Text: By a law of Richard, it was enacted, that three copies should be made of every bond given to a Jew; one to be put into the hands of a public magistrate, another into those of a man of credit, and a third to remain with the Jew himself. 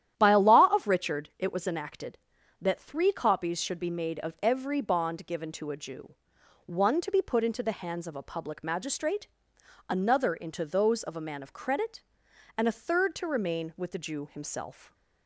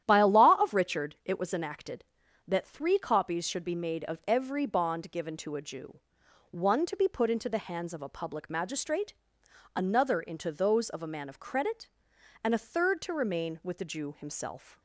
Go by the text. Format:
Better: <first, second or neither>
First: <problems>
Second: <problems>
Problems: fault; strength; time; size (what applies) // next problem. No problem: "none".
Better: neither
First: starts louder than the rest; strong; until 1.1 s; 11 dB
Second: starts louder than the rest; strong; until 1.0 s; 11 dB